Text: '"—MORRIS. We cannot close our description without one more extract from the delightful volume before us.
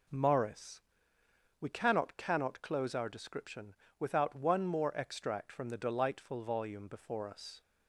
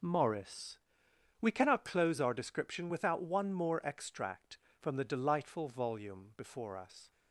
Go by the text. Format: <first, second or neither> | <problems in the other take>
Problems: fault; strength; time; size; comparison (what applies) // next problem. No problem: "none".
second | says "cannot" twice; at 2.1 s // pauses between "description" and "without"; slight; at 3.7 s; 0.24 s long